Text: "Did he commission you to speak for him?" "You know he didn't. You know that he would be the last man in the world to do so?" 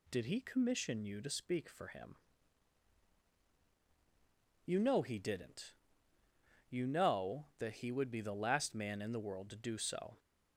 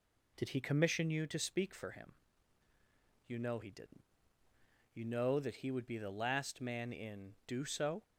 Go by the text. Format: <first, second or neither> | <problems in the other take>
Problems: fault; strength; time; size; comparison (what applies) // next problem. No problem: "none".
first | skips "the world to"; at 7.4 s